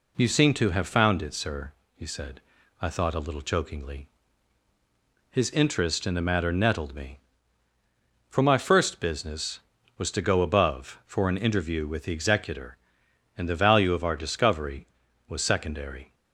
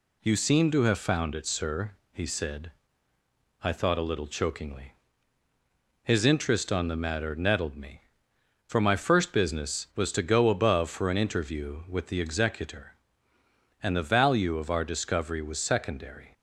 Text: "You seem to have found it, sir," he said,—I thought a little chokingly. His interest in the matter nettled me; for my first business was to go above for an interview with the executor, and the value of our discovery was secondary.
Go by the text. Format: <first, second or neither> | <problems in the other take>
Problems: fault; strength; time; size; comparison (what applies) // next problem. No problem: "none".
first | says "on" for "in"; at 6.7 s